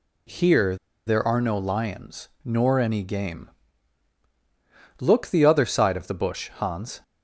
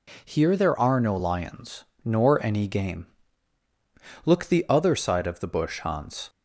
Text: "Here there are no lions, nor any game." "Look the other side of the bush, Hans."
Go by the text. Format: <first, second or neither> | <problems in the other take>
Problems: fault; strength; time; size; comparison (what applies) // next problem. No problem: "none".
second | pauses between "Here" and "there"; slight; at 0.7 s; 0.30 s long